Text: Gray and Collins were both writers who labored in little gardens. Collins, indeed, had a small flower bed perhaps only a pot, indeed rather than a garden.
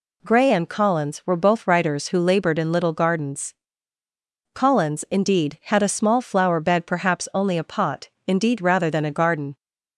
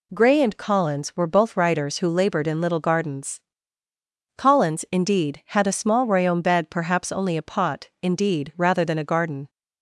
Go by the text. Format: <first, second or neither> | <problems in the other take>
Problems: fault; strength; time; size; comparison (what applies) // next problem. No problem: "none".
first | says "royaume" for "flower"; at 6.0 s